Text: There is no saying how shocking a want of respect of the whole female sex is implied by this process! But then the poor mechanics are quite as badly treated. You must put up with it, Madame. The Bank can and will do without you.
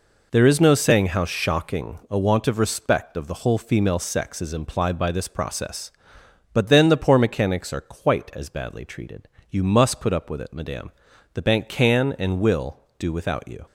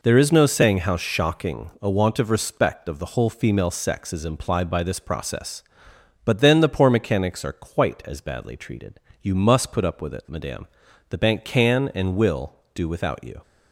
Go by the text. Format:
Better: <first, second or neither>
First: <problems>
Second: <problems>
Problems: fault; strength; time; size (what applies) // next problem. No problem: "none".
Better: neither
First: none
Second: none